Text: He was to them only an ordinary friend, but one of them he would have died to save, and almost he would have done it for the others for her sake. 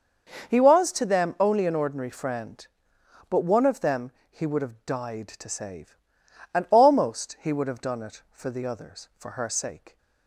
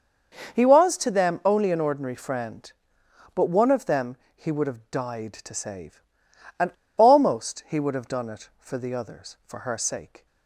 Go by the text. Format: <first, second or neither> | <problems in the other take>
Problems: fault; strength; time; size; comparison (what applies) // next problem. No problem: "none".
first | starts louder than the rest; until 1.6 s; 6 dB; also in the first // pauses between "them" and "he"; slight; at 4.1 s; 0.20 s long; slight in the first // pauses between "and" and "almost"; slight; at 6.7 s; 0.25 s long